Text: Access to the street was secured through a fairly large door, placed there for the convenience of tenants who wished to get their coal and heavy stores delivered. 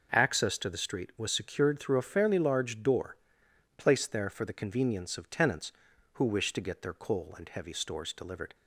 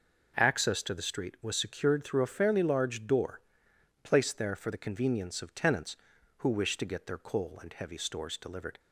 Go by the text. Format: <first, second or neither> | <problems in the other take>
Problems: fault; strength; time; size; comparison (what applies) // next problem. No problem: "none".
neither | none